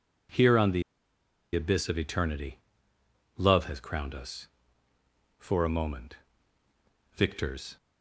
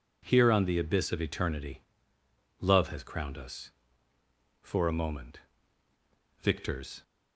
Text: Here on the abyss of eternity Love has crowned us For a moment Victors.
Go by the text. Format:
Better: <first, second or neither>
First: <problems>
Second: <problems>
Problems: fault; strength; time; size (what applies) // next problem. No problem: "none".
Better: second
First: pauses between "the" and "abyss"; noticeable; at 0.8 s; 0.71 s long // pauses between "eternity" and "Love"; noticeable; at 2.5 s; 0.80 s long // pauses between "moment" and "Victors"; at 6.1 s; 1.0 s long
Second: pauses between "eternity" and "Love"; noticeable; at 1.8 s; 0.80 s long // pauses between "moment" and "Victors"; at 5.3 s; 1.0 s long